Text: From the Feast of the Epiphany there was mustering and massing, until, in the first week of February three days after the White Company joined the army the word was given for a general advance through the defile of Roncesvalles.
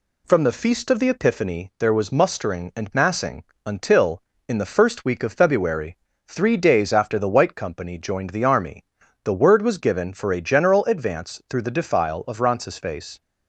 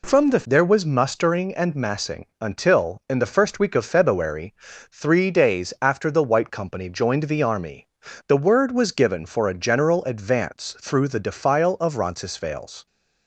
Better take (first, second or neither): first